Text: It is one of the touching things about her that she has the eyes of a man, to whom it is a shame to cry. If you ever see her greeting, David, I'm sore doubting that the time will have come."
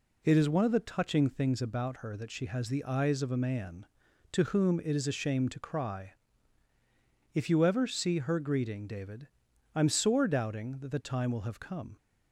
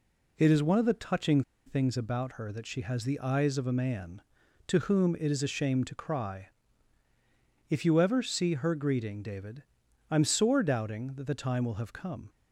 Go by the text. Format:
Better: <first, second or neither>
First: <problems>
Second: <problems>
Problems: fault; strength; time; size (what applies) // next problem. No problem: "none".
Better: first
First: none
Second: pauses between "touching" and "things"; slight; at 1.4 s; 0.24 s long